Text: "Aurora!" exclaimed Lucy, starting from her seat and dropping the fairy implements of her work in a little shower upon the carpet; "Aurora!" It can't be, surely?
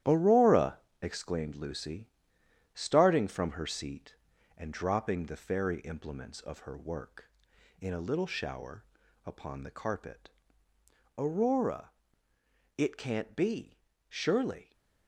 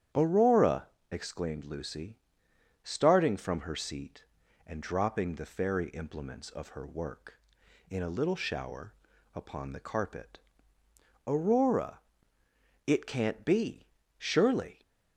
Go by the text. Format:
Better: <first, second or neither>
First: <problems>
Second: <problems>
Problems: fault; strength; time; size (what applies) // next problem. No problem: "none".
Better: second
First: gets quieter; strong; throughout; 8 dB // starts louder than the rest; strong; until 1.2 s; 12 dB // pauses between "shower" and "upon"; at 8.8 s; 0.42 s long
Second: starts louder than the rest; strong; until 1.4 s; 10 dB // pauses between "shower" and "upon"; at 8.9 s; 0.42 s long